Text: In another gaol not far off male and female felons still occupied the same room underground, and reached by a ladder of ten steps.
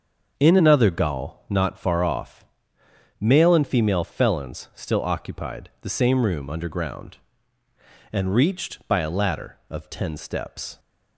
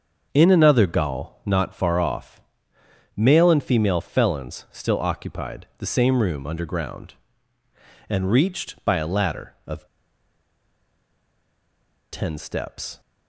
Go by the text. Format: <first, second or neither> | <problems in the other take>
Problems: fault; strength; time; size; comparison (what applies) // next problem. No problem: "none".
first | starts louder than the rest; until 1.3 s; 6.5 dB; also in the first // pauses between "off" and "male"; noticeable; at 2.3 s; 0.76 s long; noticeable in the first // pauses between "of" and "ten"; strong; at 9.8 s; 2.2 s long